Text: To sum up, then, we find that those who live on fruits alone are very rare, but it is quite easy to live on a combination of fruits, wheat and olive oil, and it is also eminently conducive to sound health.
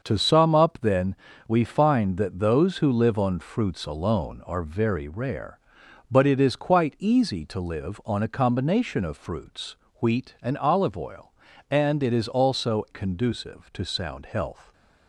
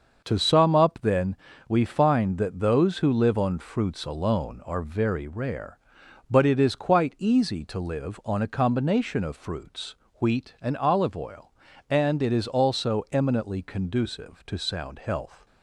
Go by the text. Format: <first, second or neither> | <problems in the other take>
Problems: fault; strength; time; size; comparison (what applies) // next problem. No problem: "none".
second | starts louder than the rest; until 1.0 s; 6.5 dB; also in the second // skips "eminently"; at 12.8 s